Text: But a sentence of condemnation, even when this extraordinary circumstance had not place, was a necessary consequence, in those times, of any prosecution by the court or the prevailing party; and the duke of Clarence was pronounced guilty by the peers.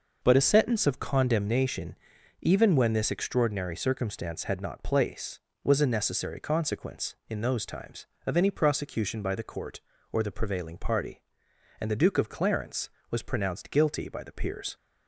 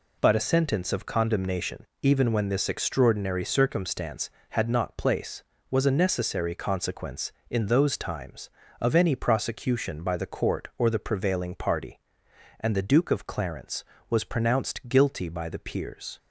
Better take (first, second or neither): neither